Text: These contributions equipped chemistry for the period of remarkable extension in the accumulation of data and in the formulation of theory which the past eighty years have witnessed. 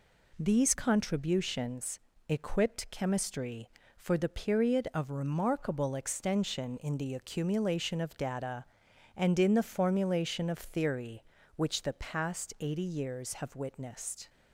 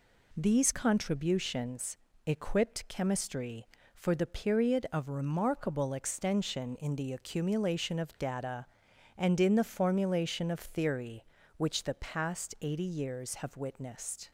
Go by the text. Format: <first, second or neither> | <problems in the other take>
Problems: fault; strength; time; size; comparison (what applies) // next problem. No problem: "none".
neither | pauses between "contributions" and "equipped"; slight; the same in both